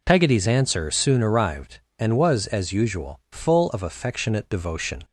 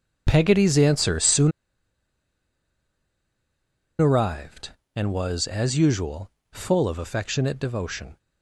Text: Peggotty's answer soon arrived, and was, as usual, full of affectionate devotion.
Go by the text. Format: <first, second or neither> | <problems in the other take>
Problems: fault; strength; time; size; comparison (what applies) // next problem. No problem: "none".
first | pauses between "soon" and "arrived"; strong; at 1.5 s; 2.5 s long